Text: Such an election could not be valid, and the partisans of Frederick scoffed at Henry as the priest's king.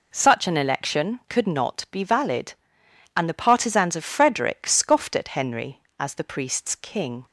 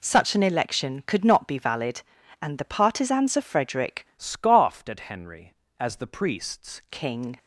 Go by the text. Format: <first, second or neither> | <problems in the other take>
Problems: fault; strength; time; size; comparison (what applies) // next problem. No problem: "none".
first | changes voice from "scoffed" to "priest's"; from 4.1 to 6.7 s; 2.6 s long